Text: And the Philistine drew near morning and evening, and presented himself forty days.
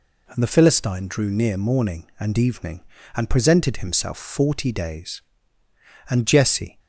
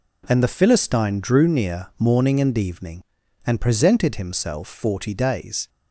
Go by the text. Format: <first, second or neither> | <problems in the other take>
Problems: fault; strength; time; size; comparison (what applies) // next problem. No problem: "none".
second | goes on to say "And Jesse"; noticeable; from 6.0 s on; 0.70 s long